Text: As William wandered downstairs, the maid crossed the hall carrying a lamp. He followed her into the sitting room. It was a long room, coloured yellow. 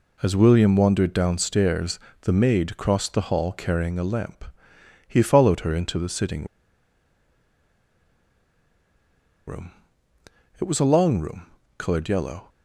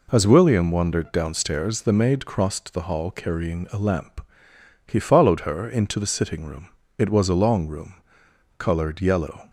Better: second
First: pauses between "sitting" and "room"; strong; at 6.4 s; 3.0 s long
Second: none

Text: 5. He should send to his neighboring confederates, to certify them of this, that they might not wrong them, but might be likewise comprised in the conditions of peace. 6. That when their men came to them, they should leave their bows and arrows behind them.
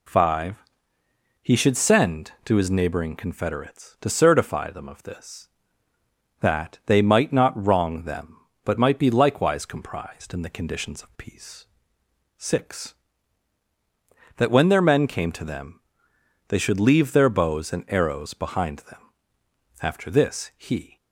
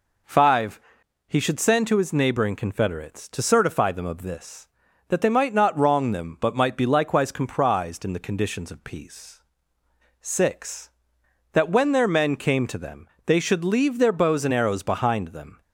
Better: second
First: goes on to say "After this he"; noticeable; from 19.7 s on; 1.1 s long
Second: none

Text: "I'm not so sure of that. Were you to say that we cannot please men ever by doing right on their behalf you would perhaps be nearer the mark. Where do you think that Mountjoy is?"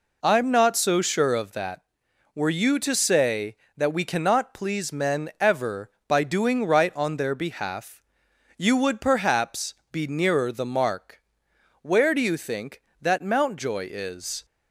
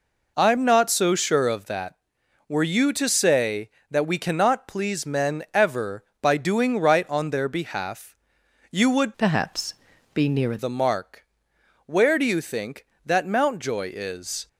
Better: first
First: pauses between "behalf" and "you"; noticeable; at 8.0 s; 0.56 s long // pauses between "perhaps" and "be"; slight; at 9.7 s; 0.16 s long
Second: pauses between "behalf" and "you"; noticeable; at 8.1 s; 0.56 s long // changes voice from "perhaps" to "nearer"; from 9.1 to 10.5 s; 1.4 s long // pauses between "perhaps" and "be"; at 9.7 s; 0.42 s long

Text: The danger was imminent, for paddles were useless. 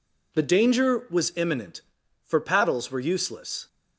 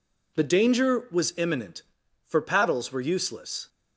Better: neither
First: none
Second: none

